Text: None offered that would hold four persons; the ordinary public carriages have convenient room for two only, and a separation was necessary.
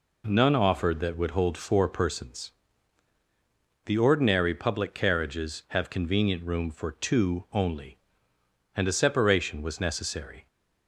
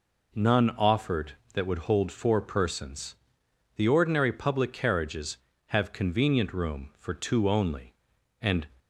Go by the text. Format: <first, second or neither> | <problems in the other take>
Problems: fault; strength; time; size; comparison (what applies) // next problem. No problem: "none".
first | stops before "a separation was necessary"; at 8.7 s